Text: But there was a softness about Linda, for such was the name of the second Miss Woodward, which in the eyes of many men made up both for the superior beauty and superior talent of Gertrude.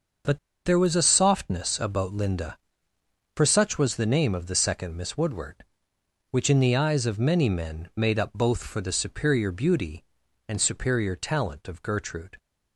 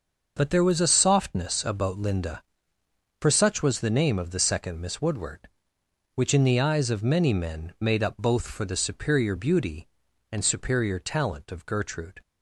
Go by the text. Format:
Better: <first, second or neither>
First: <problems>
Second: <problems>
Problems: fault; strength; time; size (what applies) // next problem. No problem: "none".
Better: second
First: starts louder than the rest; until 1.5 s; 6.5 dB // pauses between "But" and "there"; slight; at 0.3 s; 0.27 s long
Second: starts louder than the rest; until 1.3 s; 6.5 dB